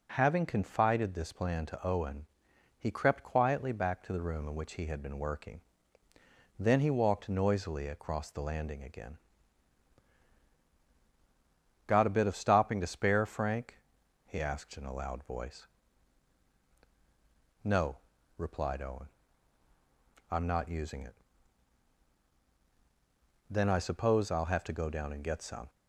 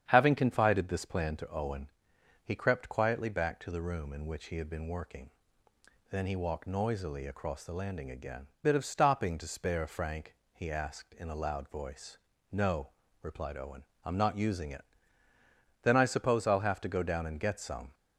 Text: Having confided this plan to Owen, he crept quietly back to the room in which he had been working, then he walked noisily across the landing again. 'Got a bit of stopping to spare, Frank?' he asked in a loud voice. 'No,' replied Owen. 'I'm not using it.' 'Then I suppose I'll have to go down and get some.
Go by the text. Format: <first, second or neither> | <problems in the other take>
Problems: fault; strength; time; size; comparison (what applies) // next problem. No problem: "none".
first | starts louder than the rest; strong; until 1.1 s; 8.5 dB // skips "Got a"; at 8.5 s